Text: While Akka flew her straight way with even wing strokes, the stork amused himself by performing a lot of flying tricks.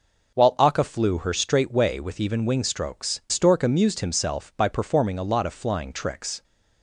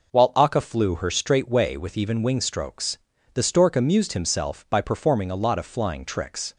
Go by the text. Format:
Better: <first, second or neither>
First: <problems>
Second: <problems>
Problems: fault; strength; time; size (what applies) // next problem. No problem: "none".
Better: second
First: skips "the"; at 3.2 s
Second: none